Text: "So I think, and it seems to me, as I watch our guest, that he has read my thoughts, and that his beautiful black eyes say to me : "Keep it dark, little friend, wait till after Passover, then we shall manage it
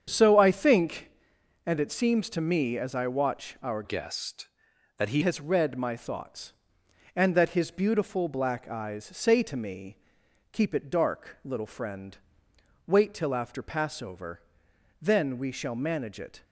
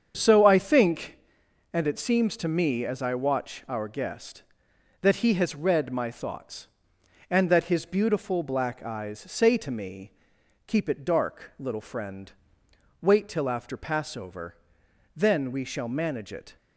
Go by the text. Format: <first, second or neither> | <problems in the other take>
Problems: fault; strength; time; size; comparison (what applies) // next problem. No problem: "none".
second | starts louder than the rest; strong; until 1.0 s; 7.5 dB; strong in the second // changes voice from "guest" to "he"; from 3.8 to 5.2 s; 1.4 s long